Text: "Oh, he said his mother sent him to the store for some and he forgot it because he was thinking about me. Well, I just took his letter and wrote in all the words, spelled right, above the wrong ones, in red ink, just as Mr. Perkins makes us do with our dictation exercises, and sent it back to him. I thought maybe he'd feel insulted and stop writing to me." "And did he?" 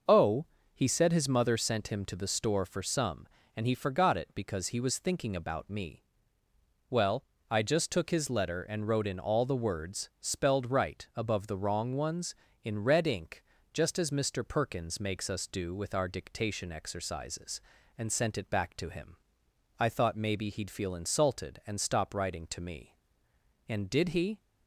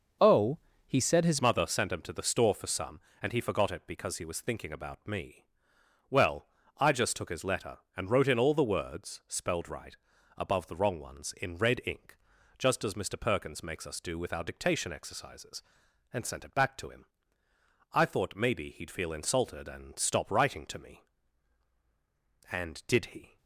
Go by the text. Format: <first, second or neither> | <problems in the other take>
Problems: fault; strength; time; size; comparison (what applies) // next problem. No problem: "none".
first | starts louder than the rest; until 1.5 s; 6 dB // changes voice at "mother"; from 1.4 s on; 21.9 s long